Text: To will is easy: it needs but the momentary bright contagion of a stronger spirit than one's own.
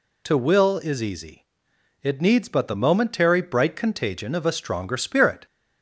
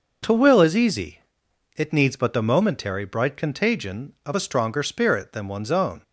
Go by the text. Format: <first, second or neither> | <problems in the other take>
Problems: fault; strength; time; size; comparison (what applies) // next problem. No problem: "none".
second | stops before "than one's own"; at 5.4 s